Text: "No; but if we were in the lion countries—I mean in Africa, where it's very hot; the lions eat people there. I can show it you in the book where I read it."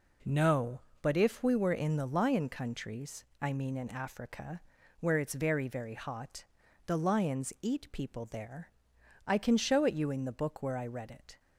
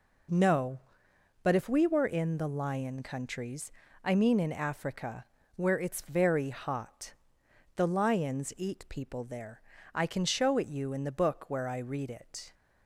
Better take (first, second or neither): second